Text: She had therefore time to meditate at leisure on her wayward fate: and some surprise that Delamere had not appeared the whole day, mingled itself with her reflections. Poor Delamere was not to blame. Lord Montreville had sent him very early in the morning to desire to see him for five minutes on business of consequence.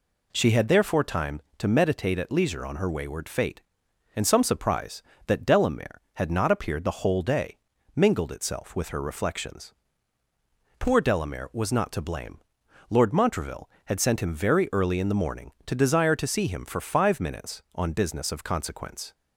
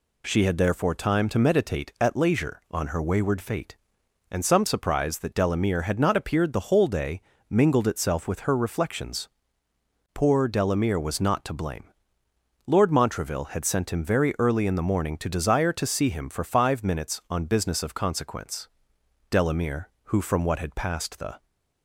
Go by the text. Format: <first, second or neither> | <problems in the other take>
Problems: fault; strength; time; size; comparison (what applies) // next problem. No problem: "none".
first | goes on to say "Delamere who from what had passed the"; strong; from 19.2 s on; 2.1 s long